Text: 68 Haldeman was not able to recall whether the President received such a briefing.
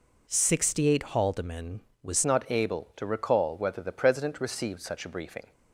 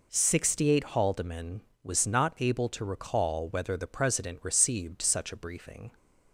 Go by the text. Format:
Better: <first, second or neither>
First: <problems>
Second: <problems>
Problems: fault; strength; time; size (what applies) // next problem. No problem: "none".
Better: second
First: changes voice at "not"; from 2.2 s on; 3.3 s long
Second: none